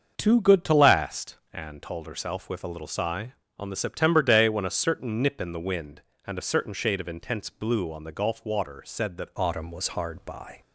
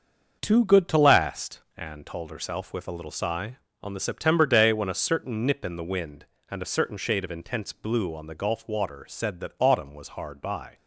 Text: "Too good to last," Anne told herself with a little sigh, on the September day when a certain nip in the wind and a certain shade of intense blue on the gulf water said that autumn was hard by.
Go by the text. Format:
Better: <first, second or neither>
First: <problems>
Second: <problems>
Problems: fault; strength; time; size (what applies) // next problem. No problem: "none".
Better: second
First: starts louder than the rest; until 1.2 s; 6.5 dB // changes voice at "autumn"; from 9.3 s on; 1.3 s long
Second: starts louder than the rest; until 1.4 s; 6.5 dB